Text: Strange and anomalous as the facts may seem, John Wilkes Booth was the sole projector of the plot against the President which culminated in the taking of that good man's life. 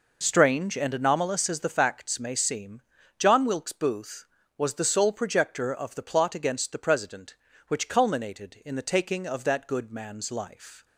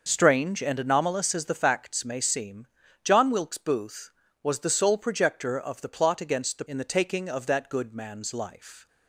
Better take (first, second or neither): first